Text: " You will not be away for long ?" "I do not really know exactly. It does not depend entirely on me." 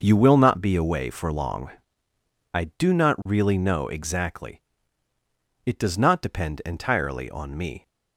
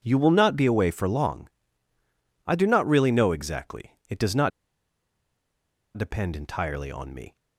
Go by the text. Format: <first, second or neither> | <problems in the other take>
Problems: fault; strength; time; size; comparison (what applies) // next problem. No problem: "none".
first | starts louder than the rest; strong; until 1.0 s; 8 dB // pauses between "not" and "depend"; strong; at 4.5 s; 1.4 s long